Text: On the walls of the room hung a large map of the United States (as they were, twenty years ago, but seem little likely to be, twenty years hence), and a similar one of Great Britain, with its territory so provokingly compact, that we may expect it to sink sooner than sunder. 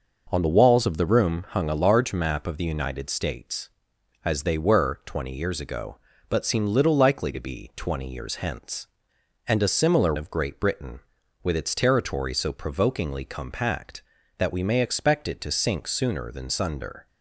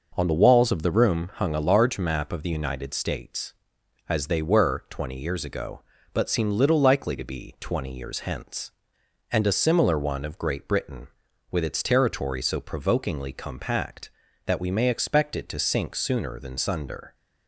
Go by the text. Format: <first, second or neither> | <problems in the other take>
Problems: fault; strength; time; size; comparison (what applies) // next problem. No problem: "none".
second | skips "one"; at 10.1 s